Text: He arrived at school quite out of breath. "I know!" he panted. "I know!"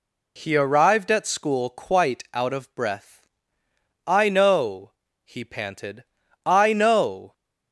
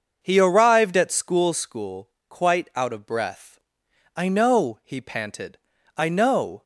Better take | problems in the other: first | starts louder than the rest; until 1.2 s; 6.5 dB // says "school" twice; at 1.5 s

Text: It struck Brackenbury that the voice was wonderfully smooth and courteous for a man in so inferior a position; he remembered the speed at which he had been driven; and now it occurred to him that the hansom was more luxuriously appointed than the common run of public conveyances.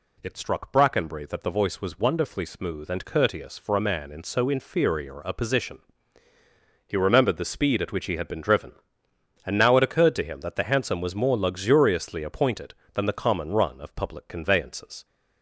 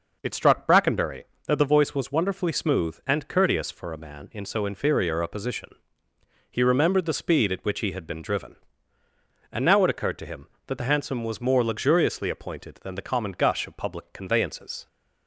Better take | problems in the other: first | says "gush" for "run"; at 13.3 s

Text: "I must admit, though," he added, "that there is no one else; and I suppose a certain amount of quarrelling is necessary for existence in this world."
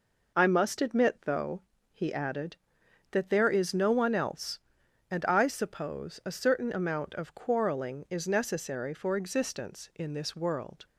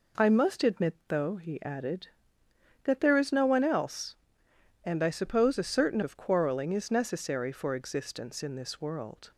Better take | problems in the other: first | skips "amount"; at 6.0 s

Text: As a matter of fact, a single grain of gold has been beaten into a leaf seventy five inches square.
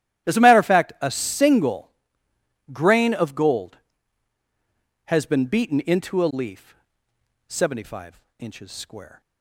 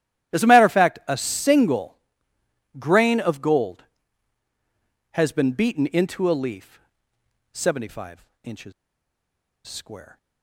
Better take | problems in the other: first | starts louder than the rest; strong; until 1.4 s; 12.5 dB; strong in the first // pauses between "single" and "grain"; noticeable; at 1.9 s; 0.82 s long; noticeable in the first // pauses between "leaf" and "seventy"; noticeable; at 6.8 s; 0.72 s long; noticeable in the first // pauses between "five" and "inches"; slight; at 8.2 s; 0.18 s long; slight in the first // pauses between "inches" and "square"; noticeable; at 8.7 s; 0.94 s long

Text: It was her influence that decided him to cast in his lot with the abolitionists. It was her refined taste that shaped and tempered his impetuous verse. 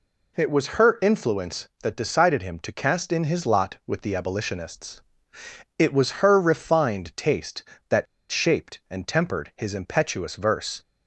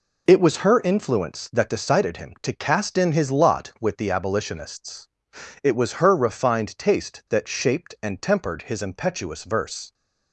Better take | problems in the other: second | pauses between "that" and "shaped"; slight; at 8.0 s; 0.25 s long

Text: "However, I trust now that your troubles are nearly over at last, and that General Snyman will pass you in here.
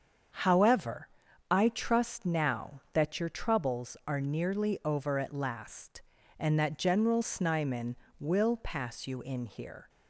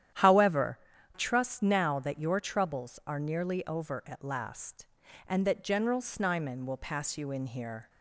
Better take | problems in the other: first | starts louder than the rest; strong; until 1.5 s; 10.5 dB; also in the first // skips "I"; at 0.9 s

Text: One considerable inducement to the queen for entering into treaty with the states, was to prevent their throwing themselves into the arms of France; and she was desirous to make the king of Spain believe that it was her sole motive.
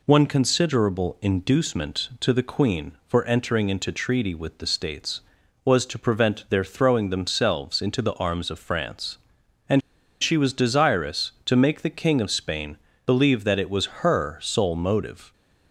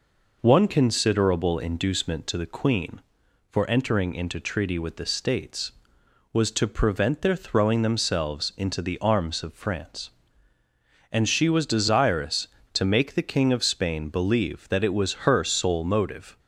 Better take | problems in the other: second | pauses between "and" and "she"; at 9.8 s; 0.40 s long // pauses between "Spain" and "believe"; slight; at 12.7 s; 0.30 s long

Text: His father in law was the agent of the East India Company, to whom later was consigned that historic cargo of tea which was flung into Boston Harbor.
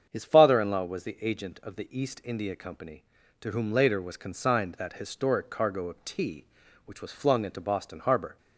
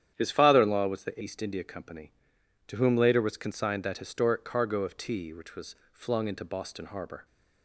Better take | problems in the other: first | starts louder than the rest; strong; until 1.1 s; 10 dB; strong in the first // skips "agent of the"; at 1.2 s // pauses between "was" and "flung"; slight; at 5.7 s; 0.16 s long

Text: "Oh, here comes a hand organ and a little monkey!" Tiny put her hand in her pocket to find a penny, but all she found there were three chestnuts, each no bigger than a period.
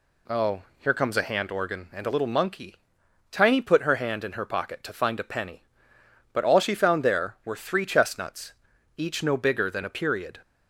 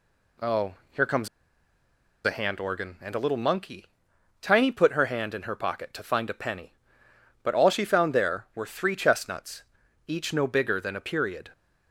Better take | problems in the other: first | pauses between "comes" and "a"; noticeable; at 1.2 s; 0.97 s long

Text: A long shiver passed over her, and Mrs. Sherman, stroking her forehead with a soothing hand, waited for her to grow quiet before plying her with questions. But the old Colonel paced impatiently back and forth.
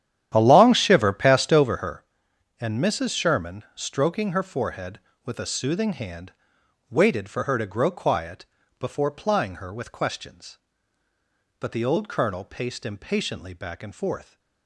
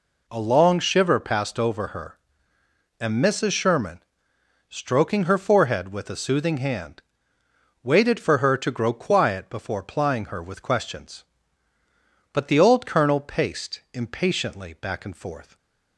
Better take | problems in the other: second | starts louder than the rest; strong; until 1.8 s; 10.5 dB // pauses between "quiet" and "before"; slight; at 8.4 s; 0.32 s long

